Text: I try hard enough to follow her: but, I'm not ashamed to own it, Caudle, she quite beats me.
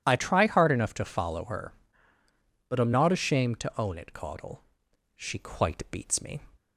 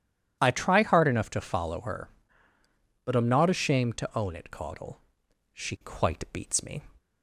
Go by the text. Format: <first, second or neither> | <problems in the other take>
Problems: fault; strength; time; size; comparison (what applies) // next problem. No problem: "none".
neither | none